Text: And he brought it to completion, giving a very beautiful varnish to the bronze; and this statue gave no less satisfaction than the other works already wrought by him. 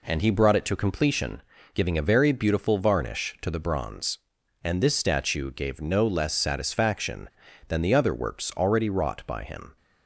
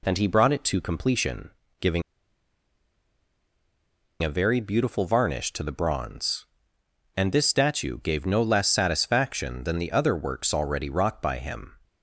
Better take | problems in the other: first | pauses between "giving" and "a"; strong; at 2.0 s; 2.2 s long

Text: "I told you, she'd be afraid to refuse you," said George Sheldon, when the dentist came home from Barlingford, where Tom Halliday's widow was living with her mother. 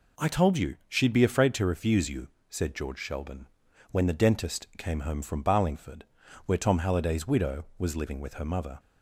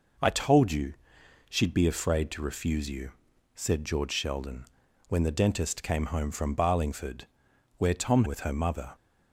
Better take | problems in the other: first | skips "Halliday's widow was living"; at 8.2 s

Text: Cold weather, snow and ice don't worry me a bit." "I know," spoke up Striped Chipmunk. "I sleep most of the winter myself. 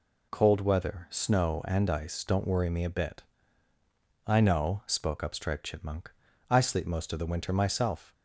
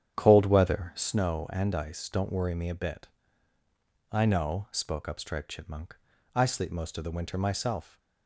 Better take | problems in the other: first | starts louder than the rest; strong; until 1.1 s; 9.5 dB

